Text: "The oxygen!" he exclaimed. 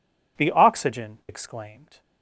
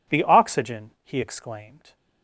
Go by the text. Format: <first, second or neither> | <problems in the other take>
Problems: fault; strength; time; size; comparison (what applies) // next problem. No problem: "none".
second | skips "he"; at 1.2 s